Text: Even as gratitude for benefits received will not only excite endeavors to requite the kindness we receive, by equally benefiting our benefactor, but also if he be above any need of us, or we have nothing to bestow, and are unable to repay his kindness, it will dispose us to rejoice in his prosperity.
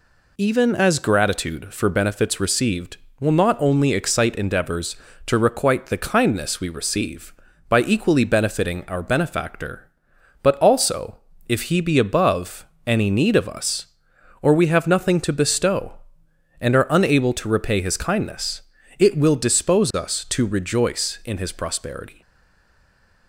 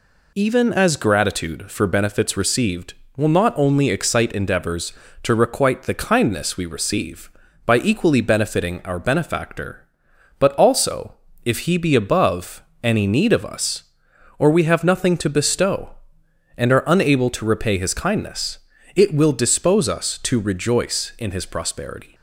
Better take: second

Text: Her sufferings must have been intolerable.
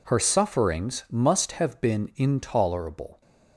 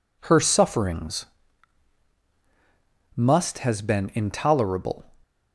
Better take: first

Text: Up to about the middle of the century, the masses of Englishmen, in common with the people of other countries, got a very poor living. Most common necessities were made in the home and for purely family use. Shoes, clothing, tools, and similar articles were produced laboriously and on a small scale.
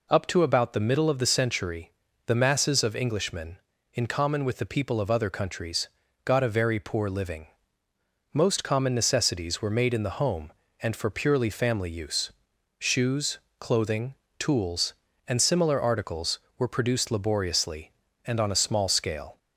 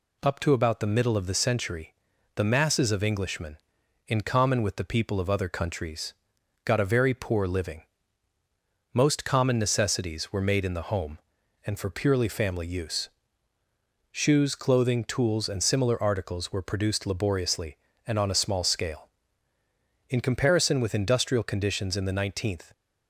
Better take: first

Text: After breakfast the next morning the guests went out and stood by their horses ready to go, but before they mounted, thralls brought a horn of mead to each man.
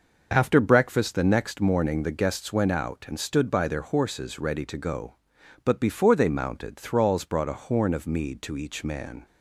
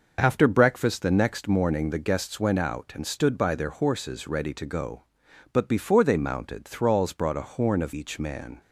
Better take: first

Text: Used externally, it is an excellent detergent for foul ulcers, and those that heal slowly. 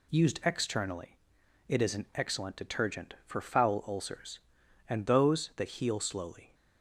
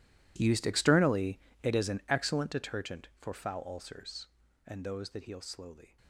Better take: first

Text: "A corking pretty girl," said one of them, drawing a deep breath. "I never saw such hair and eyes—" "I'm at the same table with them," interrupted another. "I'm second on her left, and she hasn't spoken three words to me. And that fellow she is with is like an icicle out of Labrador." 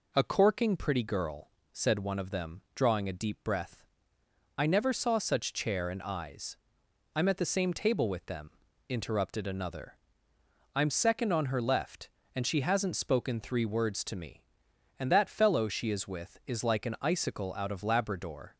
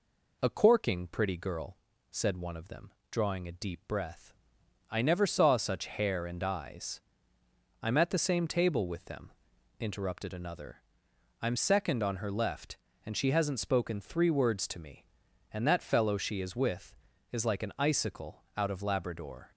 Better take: second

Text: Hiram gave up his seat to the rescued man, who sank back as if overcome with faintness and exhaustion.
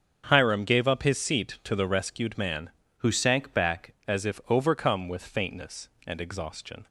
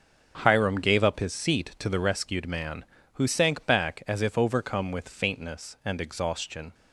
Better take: second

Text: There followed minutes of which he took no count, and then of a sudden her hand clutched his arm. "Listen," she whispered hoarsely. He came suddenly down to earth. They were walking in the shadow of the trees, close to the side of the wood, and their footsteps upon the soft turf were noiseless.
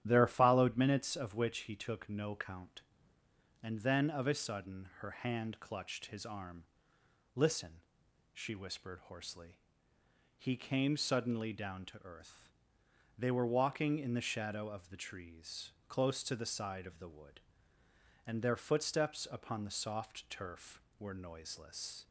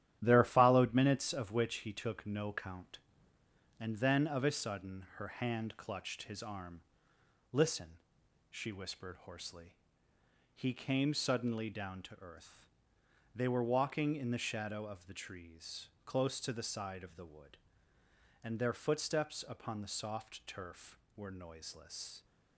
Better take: first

